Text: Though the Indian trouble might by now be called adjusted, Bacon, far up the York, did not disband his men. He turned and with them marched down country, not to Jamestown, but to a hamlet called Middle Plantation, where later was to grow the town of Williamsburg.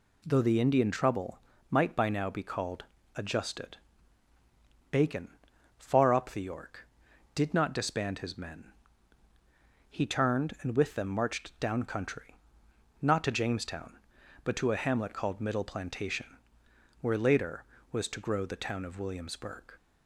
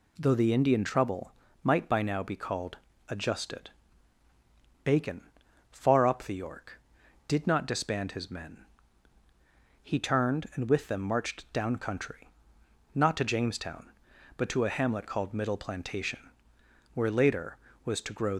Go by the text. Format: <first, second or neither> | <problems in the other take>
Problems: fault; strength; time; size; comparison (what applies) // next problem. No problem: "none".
first | pauses between "trouble" and "might"; slight; at 1.3 s; 0.30 s long; slight in the first // pauses between "called" and "adjusted"; slight; at 2.7 s; 0.32 s long; slight in the first // stops before "the town of Williamsburg"; at 18.3 s